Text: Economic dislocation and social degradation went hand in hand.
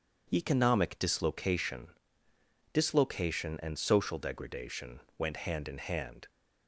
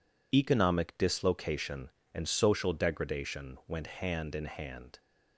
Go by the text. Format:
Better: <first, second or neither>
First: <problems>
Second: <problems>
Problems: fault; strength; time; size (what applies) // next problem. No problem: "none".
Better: second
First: says "dislocation" twice; at 2.7 s // pauses between "degradation" and "went"; slight; at 5.0 s; 0.16 s long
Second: none